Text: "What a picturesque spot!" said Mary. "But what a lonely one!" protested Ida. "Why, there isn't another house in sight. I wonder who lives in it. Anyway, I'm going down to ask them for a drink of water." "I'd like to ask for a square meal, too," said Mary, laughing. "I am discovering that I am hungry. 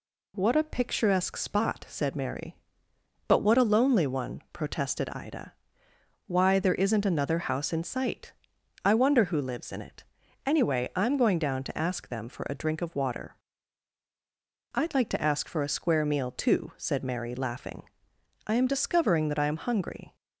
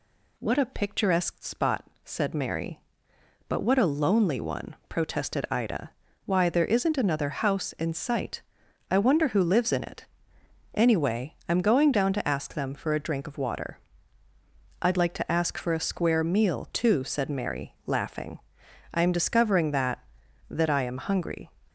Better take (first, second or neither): first